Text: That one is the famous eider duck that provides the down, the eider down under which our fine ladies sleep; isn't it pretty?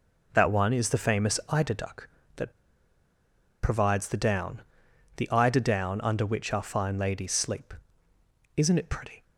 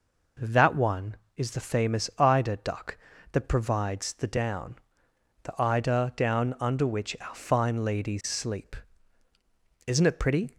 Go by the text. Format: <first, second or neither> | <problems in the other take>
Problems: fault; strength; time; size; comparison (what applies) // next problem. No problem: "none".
second | pauses between "that" and "provides"; at 2.5 s; 1.1 s long